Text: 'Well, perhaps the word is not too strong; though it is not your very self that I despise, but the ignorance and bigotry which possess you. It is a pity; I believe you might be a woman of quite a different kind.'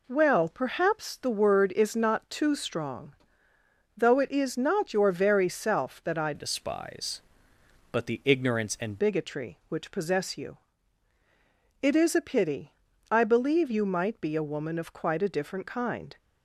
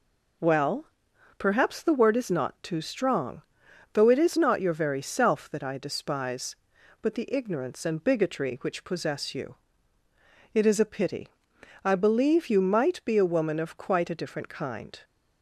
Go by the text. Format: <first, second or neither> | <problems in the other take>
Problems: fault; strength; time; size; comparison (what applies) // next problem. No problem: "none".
second | changes voice from "despise" to "and"; from 6.3 to 9.0 s; 2.7 s long